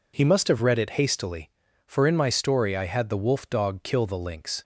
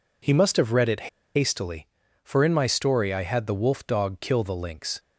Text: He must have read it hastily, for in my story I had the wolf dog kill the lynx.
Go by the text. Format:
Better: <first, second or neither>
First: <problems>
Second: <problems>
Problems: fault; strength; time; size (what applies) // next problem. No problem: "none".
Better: first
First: none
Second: pauses between "it" and "hastily"; slight; at 1.0 s; 0.27 s long